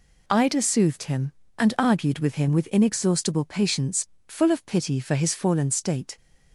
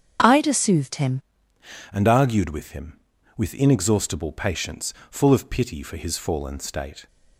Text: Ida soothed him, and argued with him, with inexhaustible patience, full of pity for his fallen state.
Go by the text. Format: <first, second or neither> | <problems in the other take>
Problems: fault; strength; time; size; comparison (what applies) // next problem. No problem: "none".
first | starts louder than the rest; strong; until 1.9 s; 7.5 dB // changes voice at "and"; from 1.9 s on; 5.1 s long